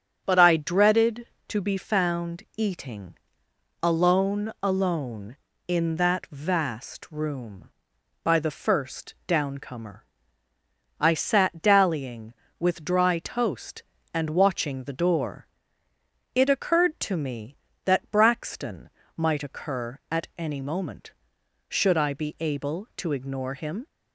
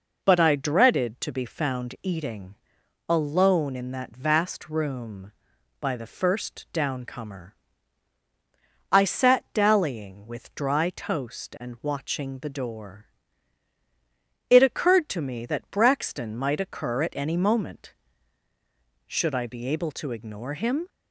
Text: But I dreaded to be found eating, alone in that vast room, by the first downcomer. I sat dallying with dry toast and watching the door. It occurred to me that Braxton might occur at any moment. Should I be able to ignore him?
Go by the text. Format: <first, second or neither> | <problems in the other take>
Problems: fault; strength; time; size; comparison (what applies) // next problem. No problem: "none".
second | starts louder than the rest; strong; until 1.2 s; 8 dB // says "alone" twice; at 4.6 s // pauses between "Braxton" and "might"; slight; at 18.9 s; 0.26 s long